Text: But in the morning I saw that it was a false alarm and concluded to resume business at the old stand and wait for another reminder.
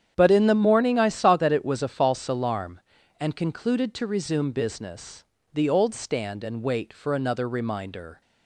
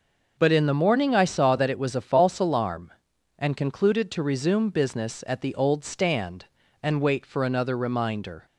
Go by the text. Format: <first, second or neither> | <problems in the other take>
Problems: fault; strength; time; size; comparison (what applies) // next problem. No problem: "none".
second | starts louder than the rest; strong; until 1.1 s; 9 dB // skips "at"; at 5.3 s